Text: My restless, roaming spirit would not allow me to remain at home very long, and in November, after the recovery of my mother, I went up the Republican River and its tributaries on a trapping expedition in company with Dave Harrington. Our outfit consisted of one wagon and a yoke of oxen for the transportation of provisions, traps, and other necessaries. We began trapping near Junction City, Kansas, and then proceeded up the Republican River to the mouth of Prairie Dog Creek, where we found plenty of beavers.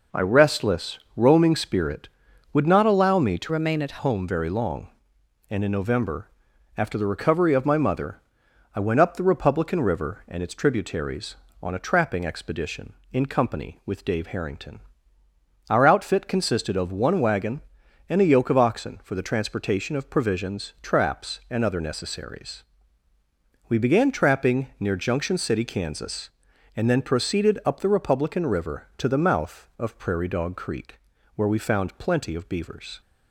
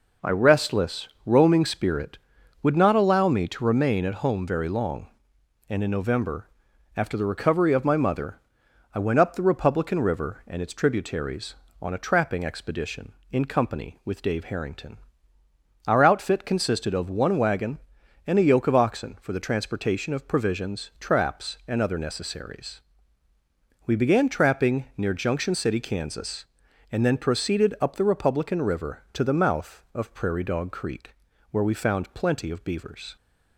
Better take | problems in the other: second | changes voice from "remain" to "at"; from 3.5 to 3.9 s; 0.4 s long

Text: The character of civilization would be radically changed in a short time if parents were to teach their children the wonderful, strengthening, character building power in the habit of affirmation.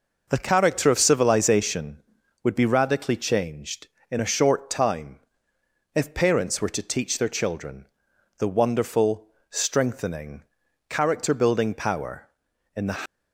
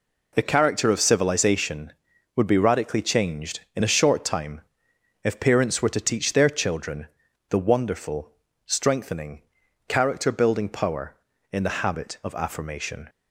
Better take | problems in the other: second | pauses between "time" and "if"; noticeable; at 5.1 s; 0.76 s long; noticeable in the second // pauses between "children" and "the"; noticeable; at 7.8 s; 0.52 s long; also in the second // stops before "habit of affirmation"; at 13.0 s

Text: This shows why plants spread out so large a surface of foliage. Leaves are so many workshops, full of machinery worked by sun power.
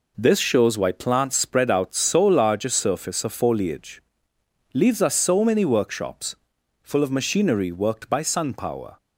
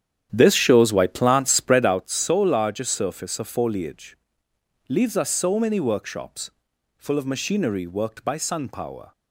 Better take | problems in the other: first | starts louder than the rest; strong; until 2.0 s; 9.5 dB

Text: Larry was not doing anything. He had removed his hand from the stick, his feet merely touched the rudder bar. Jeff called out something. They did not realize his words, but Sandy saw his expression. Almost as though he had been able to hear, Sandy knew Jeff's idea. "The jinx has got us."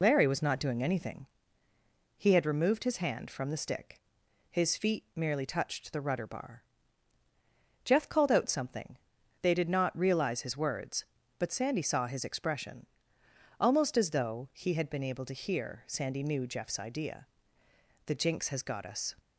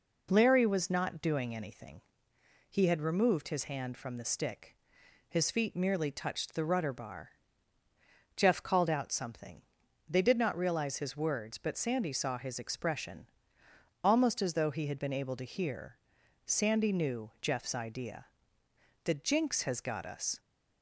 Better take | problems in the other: second | loses the start of "Larry"; at 0.0 s; 50 ms

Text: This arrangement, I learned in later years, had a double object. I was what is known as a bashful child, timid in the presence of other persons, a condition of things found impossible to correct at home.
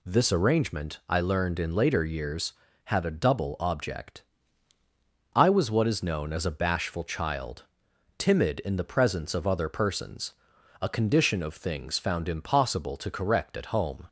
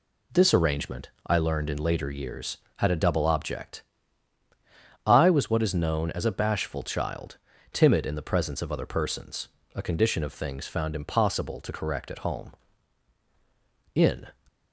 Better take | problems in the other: first | goes on to say "In"; slight; from 13.9 s on; 0.34 s long

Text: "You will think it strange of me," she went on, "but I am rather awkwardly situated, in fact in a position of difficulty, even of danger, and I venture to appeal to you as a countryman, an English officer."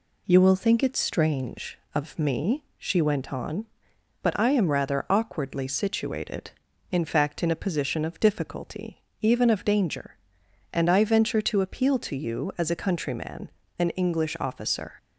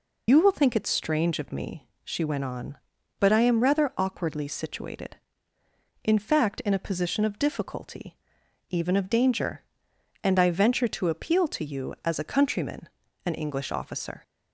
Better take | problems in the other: first | loses the start of "You"; at 0.2 s; 105 ms

